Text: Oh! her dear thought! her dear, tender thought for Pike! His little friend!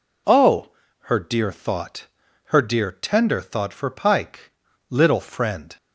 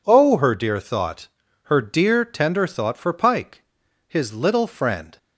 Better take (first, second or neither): second